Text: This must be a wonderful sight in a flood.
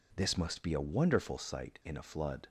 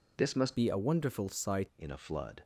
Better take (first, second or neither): first